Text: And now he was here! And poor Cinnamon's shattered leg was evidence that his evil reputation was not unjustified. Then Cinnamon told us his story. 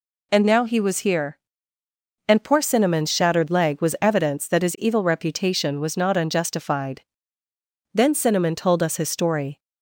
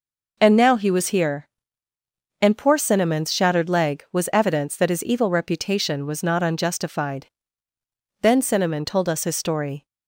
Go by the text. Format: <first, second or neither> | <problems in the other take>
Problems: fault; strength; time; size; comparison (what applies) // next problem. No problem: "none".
neither | none